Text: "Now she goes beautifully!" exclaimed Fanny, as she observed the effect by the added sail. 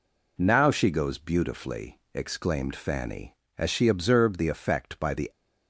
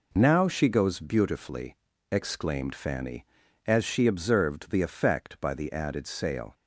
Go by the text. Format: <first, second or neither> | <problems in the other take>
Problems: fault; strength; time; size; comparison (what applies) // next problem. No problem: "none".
second | stops before "added sail"; at 5.3 s